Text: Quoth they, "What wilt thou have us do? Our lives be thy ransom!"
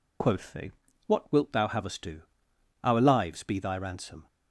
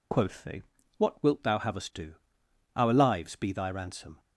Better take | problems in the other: neither | none

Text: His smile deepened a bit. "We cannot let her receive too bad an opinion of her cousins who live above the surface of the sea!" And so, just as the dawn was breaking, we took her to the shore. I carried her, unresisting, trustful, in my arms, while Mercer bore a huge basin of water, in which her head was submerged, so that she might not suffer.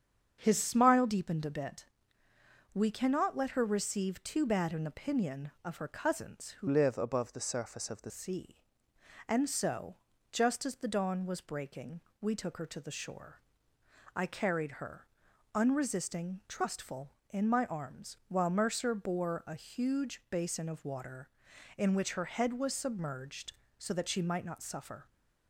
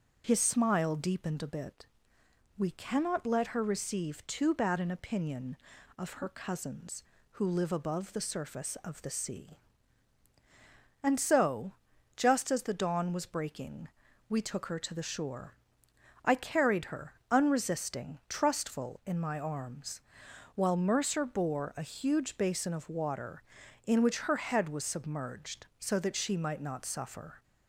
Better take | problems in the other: second | starts louder than the rest; strong; until 1.4 s; 7.5 dB; noticeable in the second // changes voice from "live" to "the"; from 6.6 to 8.1 s; 1.5 s long

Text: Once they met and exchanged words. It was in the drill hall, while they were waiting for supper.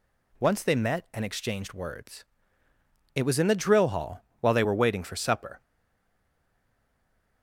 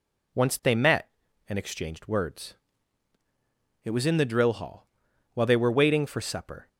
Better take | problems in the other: second | stays silent after the last word; noticeable; from 5.6 s on; 1.8 s long

